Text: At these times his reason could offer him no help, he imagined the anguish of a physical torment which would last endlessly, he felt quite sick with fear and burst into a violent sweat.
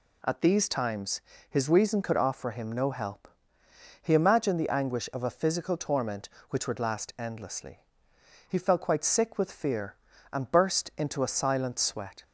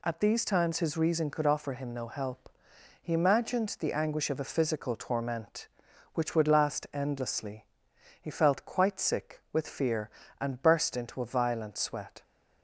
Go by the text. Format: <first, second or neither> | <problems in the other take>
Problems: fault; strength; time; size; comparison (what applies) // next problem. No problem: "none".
second | pauses between "times" and "his"; slight; at 1.1 s; 0.30 s long // says "silent" for "violent"; at 11.3 s